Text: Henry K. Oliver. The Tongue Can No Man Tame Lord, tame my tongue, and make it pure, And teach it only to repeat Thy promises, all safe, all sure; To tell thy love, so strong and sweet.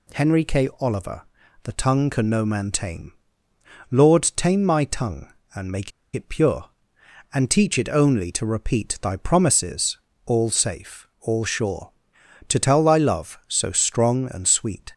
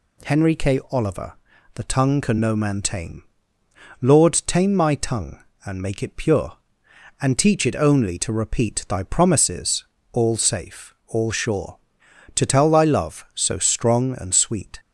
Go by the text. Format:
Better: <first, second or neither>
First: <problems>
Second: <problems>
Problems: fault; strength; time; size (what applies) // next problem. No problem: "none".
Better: second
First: pauses between "Tame" and "Lord"; noticeable; at 3.1 s; 0.78 s long // pauses between "make" and "it"; slight; at 5.9 s; 0.24 s long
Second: pauses between "Tame" and "Lord"; noticeable; at 3.2 s; 0.78 s long